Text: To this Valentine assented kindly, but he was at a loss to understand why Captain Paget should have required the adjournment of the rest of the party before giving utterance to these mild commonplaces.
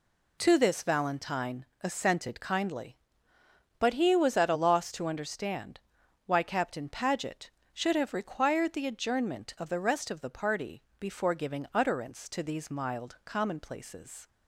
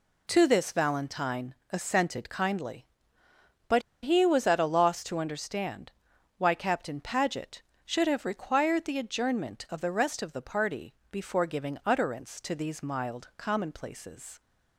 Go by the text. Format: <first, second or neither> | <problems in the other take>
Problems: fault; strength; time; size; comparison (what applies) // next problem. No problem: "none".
first | pauses between "Valentine" and "assented"; slight; at 1.5 s; 0.16 s long; slight in the first // pauses between "but" and "he"; slight; at 3.8 s; 0.21 s long // pauses between "understand" and "why"; noticeable; at 5.9 s; 0.46 s long; noticeable in the first // pauses between "party" and "before"; slight; at 10.9 s; 0.18 s long; slight in the first